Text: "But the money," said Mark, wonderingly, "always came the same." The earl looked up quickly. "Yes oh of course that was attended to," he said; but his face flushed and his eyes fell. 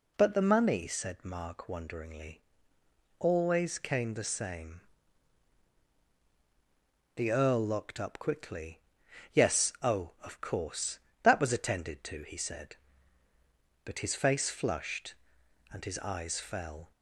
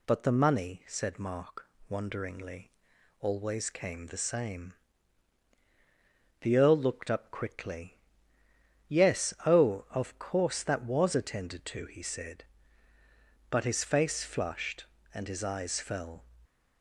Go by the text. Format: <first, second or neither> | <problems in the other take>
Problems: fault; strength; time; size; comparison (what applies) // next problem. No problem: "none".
second | says "locked" for "looked"; at 7.6 s